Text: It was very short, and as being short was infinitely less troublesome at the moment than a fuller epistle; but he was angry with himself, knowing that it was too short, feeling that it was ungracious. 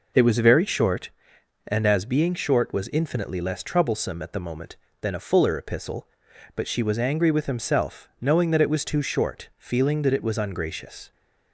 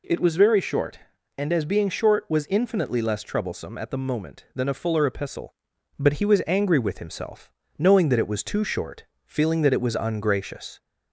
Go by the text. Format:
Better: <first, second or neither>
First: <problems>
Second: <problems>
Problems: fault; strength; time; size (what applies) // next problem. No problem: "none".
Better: second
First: says "she" for "he"; at 6.6 s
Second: none